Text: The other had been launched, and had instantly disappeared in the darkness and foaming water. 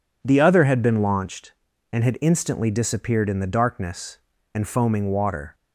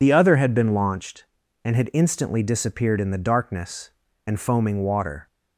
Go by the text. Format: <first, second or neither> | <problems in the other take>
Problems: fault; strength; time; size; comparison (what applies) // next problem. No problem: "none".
first | loses the start of "The"; at 0.0 s; 55 ms